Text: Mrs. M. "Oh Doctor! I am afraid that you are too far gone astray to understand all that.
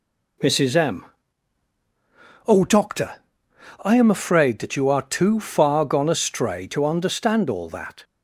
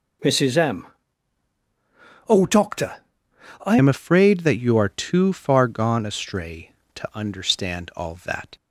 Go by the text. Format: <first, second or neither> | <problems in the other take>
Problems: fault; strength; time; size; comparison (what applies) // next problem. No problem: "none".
first | changes voice at "am"; from 3.7 s on; 4.8 s long